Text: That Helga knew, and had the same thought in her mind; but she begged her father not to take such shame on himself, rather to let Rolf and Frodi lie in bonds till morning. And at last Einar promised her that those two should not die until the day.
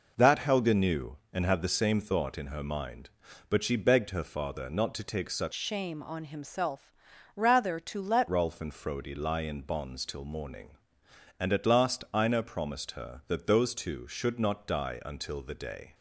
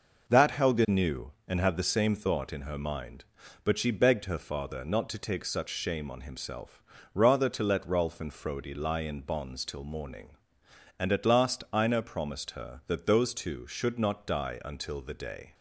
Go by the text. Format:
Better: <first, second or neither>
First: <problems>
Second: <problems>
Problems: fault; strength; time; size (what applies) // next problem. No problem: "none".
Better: second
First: changes voice from "shame" to "let"; from 5.5 to 8.2 s; 2.7 s long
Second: none